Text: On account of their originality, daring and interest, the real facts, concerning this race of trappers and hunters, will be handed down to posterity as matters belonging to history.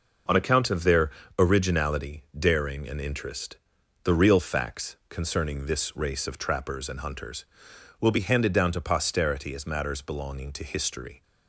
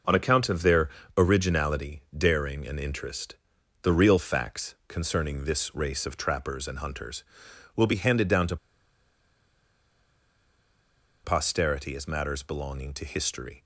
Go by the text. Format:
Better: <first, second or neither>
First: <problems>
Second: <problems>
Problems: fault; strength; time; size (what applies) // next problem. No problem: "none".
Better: first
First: pauses between "their" and "originality"; slight; at 1.0 s; 0.30 s long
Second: pauses between "their" and "originality"; slight; at 0.8 s; 0.30 s long // pauses between "to" and "posterity"; strong; at 8.5 s; 2.6 s long